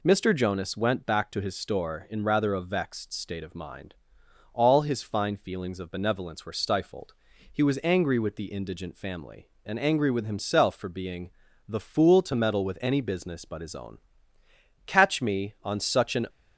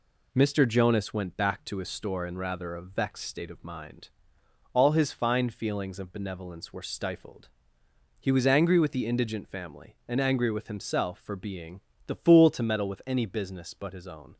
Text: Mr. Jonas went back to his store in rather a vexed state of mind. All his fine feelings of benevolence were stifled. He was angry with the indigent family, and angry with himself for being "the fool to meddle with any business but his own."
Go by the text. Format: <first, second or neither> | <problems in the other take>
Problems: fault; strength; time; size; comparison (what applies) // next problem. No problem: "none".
second | pauses between "being" and "the"; slight; at 11.3 s; 0.36 s long; slight in the second // goes on to say "Catch me on such an"; from 14.8 s on; 1.4 s long